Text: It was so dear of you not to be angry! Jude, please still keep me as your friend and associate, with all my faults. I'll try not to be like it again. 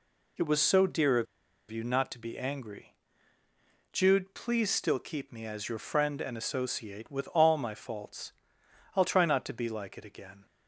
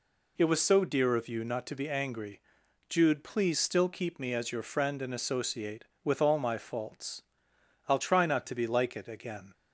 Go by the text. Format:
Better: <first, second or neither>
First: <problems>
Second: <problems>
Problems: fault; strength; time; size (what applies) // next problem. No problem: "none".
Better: second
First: pauses between "of" and "you"; at 1.2 s; 0.45 s long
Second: none